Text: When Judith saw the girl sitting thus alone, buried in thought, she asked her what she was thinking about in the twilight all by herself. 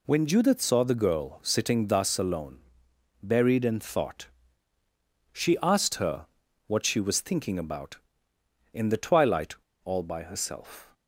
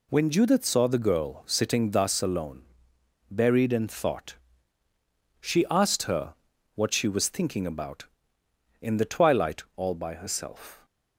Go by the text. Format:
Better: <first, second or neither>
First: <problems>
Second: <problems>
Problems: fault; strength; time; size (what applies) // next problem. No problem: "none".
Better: second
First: pauses between "her" and "what"; at 6.2 s; 0.40 s long // pauses between "twilight" and "all"; slight; at 9.5 s; 0.28 s long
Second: pauses between "her" and "what"; at 6.3 s; 0.40 s long